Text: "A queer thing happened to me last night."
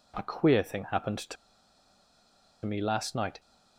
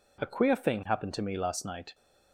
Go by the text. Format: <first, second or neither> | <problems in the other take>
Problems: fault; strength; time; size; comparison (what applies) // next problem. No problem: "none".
second | pauses between "to" and "me"; strong; at 1.3 s; 1.3 s long